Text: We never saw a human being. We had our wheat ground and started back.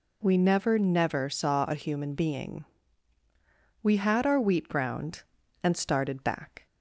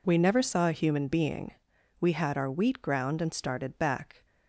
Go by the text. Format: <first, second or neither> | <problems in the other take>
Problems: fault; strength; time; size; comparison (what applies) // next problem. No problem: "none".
second | says "never" twice; at 0.7 s